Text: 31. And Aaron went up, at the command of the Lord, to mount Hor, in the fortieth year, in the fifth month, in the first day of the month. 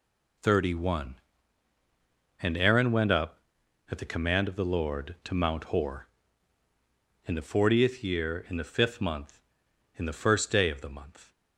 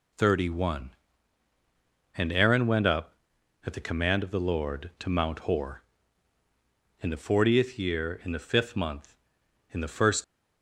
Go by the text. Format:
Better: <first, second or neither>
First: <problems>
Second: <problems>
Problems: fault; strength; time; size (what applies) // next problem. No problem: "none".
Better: first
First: none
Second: stops before "day of the month"; at 10.2 s